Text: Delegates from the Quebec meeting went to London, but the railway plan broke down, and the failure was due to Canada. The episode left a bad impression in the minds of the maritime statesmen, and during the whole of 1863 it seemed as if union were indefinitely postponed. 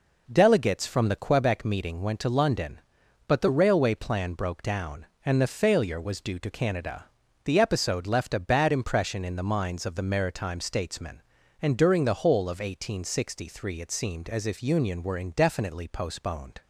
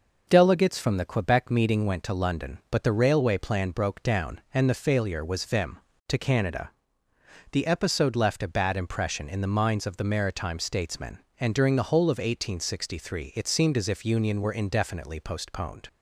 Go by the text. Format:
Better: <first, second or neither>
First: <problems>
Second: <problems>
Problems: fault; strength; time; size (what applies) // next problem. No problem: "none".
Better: first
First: none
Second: says "vim" for "due"; at 5.4 s